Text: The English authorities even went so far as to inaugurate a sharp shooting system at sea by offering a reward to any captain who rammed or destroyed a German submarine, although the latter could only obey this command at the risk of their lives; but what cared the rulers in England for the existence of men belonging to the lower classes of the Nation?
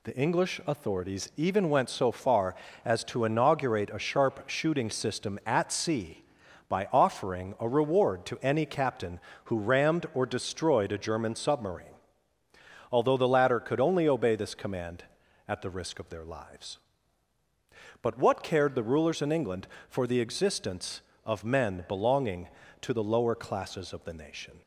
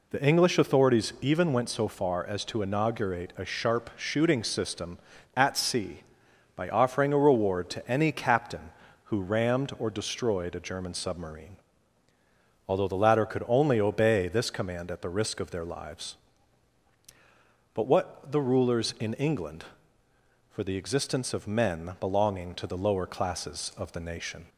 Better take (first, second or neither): first